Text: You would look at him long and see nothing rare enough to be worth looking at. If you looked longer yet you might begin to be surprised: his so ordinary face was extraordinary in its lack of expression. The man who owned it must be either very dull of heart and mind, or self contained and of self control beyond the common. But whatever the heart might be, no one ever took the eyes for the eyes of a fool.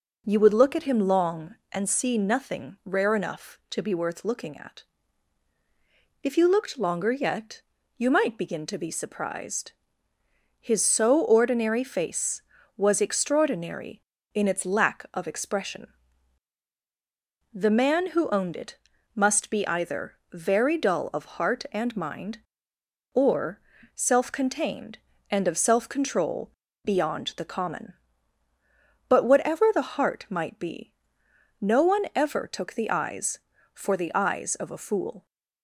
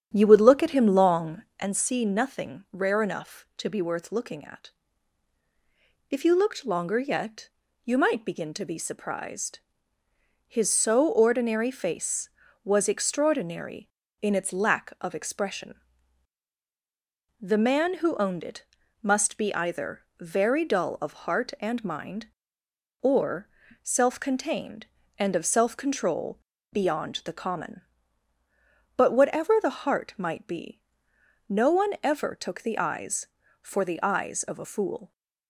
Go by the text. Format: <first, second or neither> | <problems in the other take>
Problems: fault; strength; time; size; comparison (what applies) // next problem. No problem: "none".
first | starts louder than the rest; strong; until 1.7 s; 9 dB // pauses between "yet" and "you"; at 7.4 s; 0.38 s long; also in the first // pauses between "it" and "must"; slight; at 18.6 s; 0.36 s long; slight in the first // pauses between "either" and "very"; slight; at 20.0 s; 0.18 s long; slight in the first // pauses between "or" and "self"; slight; at 23.4 s; 0.34 s long; slight in the first // pauses between "control" and "beyond"; slight; at 26.3 s; 0.36 s long; slight in the first